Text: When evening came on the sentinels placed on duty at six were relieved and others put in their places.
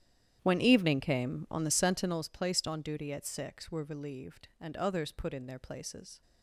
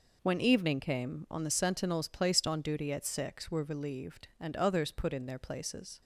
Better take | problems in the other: second | starts louder than the rest; strong; until 2.3 s; 10.5 dB

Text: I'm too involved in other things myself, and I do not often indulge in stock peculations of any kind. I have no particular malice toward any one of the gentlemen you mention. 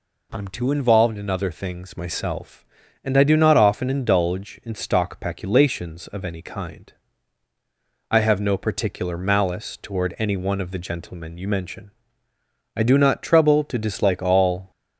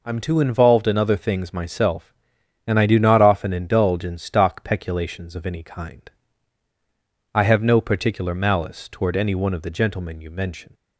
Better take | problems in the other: second | goes on to say "I do not trouble to dislike all"; strong; from 12.7 s on; 1.9 s long

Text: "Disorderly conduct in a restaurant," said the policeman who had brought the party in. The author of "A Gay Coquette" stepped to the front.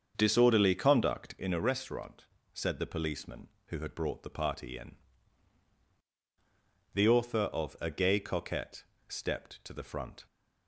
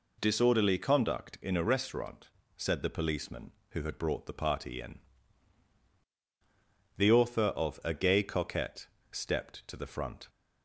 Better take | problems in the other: second | starts louder than the rest; until 1.5 s; 6.5 dB // pauses between "Coquette" and "stepped"; slight; at 8.8 s; 0.26 s long; slight in the second

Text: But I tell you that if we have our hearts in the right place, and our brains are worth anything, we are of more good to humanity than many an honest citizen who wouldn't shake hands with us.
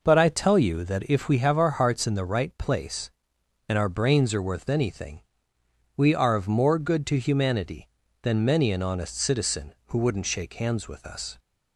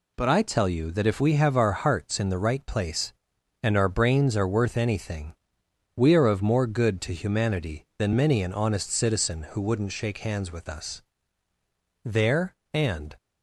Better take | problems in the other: first | goes on to say "There and"; noticeable; from 12.0 s on; 1.1 s long

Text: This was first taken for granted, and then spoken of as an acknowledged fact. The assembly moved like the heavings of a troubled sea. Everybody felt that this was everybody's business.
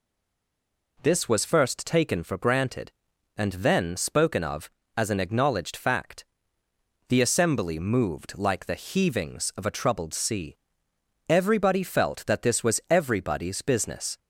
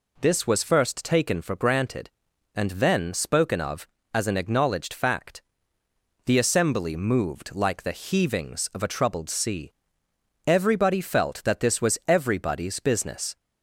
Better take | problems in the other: second | stays silent before the first word; until 0.9 s; 0.9 s long

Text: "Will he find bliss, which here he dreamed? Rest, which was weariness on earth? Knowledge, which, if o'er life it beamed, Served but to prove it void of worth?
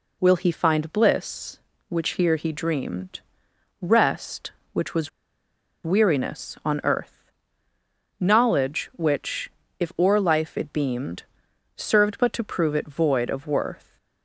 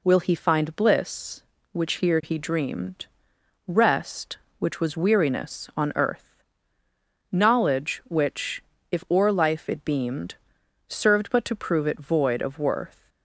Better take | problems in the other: second | pauses between "was" and "weariness"; noticeable; at 5.0 s; 0.74 s long

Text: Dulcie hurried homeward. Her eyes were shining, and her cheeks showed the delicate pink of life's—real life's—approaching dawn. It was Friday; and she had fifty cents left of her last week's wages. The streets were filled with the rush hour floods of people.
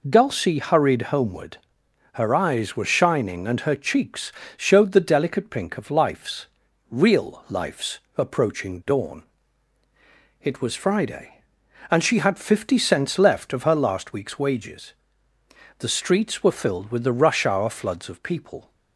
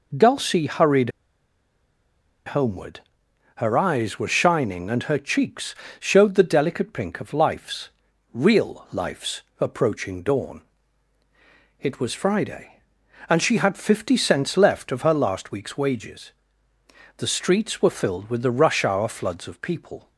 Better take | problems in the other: first | pauses between "hurried" and "homeward"; strong; at 1.0 s; 1.3 s long // pauses between "cheeks" and "showed"; slight; at 5.7 s; 0.24 s long; slight in the first

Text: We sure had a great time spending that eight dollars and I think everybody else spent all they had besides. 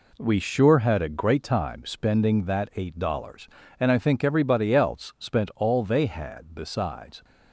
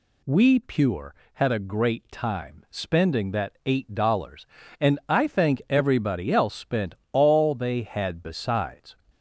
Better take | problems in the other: first | says "pure" for "sure"; at 0.5 s // pauses between "spent" and "all"; slight; at 6.9 s; 0.16 s long

